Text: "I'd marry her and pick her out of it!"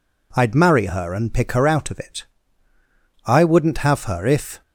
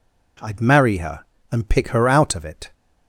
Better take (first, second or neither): second